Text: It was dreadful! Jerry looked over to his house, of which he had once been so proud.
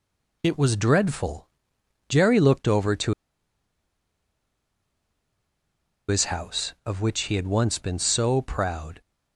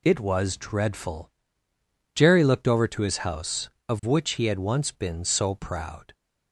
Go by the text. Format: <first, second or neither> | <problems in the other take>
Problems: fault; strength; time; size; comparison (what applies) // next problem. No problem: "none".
second | pauses between "to" and "his"; strong; at 3.1 s; 2.9 s long